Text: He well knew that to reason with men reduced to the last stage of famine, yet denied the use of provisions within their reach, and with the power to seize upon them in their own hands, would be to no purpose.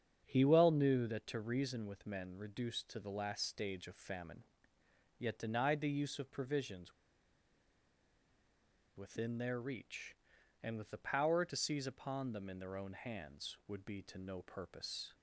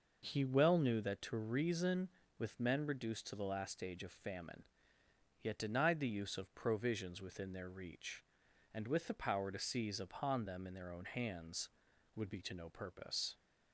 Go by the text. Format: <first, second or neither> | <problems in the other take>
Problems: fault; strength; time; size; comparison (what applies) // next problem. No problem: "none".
second | starts louder than the rest; strong; until 1.2 s; 7.5 dB // pauses between "provisions" and "within"; strong; at 6.9 s; 2.0 s long